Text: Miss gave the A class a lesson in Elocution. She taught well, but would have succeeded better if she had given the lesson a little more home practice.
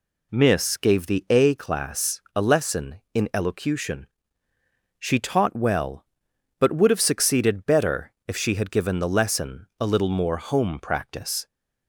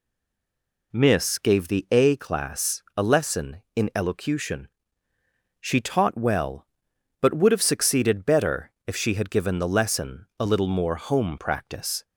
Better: first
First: pauses between "better" and "if"; slight; at 8.1 s; 0.16 s long // pauses between "lesson" and "a"; slight; at 9.6 s; 0.16 s long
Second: stays silent before the first word; slight; until 0.9 s; 0.9 s long // pauses between "better" and "if"; slight; at 8.7 s; 0.16 s long // pauses between "lesson" and "a"; slight; at 10.2 s; 0.16 s long

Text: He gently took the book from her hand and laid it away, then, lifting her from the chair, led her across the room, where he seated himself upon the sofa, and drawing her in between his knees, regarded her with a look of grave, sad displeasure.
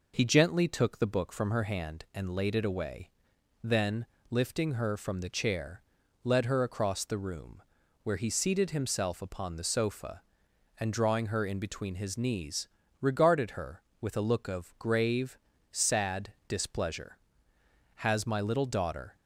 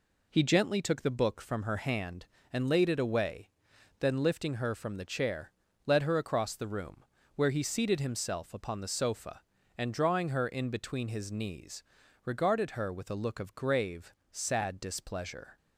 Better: second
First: goes on to say "Has my little daughter"; noticeable; from 17.9 s on; 1.2 s long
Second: none

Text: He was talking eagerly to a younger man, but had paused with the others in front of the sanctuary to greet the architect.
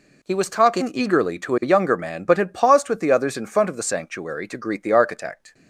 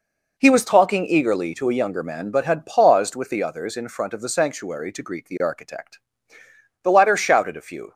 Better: first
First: none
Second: goes on to say "The latter shouted a few"; noticeable; from 6.8 s on; 1.1 s long

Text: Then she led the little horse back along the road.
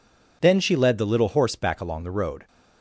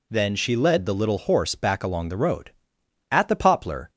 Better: first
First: none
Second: goes on to say "At the poplar"; noticeable; from 3.1 s on; 0.80 s long

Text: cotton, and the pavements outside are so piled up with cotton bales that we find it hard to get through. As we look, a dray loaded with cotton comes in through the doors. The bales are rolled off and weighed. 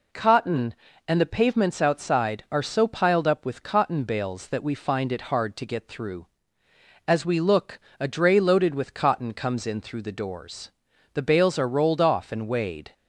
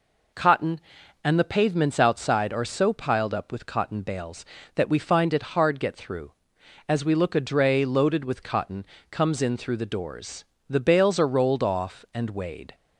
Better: first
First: none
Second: skips "to"; at 5.7 s // pauses between "cotton" and "comes"; slight; at 8.8 s; 0.26 s long

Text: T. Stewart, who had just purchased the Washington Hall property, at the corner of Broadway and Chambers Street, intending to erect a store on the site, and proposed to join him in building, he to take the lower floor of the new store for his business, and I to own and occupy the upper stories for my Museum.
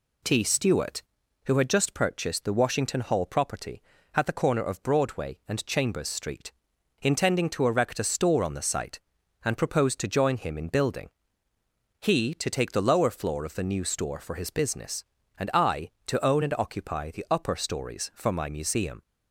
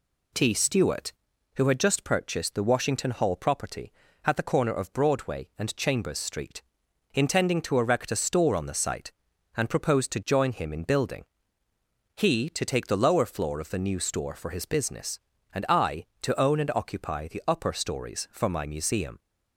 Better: neither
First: none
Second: none

